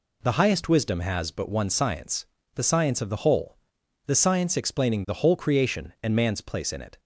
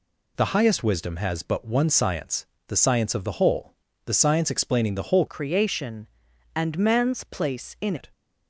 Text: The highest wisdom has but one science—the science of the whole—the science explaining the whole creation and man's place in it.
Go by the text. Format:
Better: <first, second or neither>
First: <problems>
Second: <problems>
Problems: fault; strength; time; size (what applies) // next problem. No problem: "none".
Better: first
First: none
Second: changes voice from "creation" to "in"; from 5.2 to 7.9 s; 2.7 s long